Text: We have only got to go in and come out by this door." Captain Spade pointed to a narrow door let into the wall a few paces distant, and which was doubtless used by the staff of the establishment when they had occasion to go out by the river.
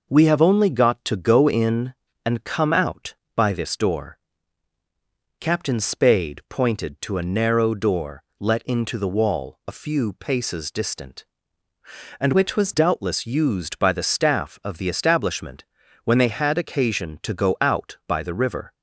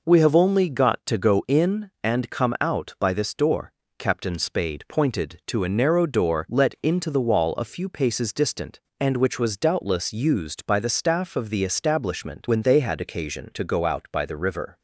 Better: second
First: pauses between "door" and "let"; slight; at 8.2 s; 0.18 s long // changes voice from "which" to "was"; from 12.3 to 12.7 s; 0.4 s long // pauses between "establishment" and "when"; at 15.6 s; 0.40 s long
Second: none

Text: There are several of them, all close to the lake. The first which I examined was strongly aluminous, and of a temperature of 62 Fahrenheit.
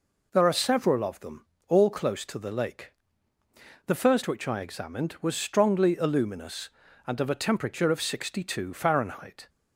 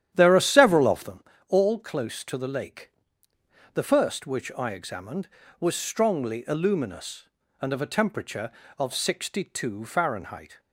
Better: first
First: none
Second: starts louder than the rest; strong; until 1.3 s; 10.5 dB

